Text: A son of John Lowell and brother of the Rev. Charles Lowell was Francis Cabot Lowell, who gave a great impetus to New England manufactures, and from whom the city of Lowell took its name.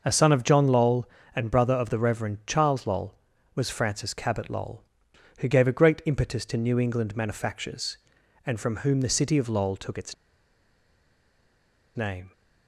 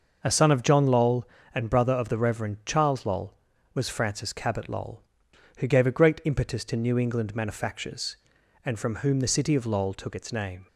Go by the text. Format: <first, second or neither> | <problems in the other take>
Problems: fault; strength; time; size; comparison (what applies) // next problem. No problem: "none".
second | starts louder than the rest; until 1.0 s; 6 dB; also in the second // pauses between "its" and "name"; strong; at 10.1 s; 1.8 s long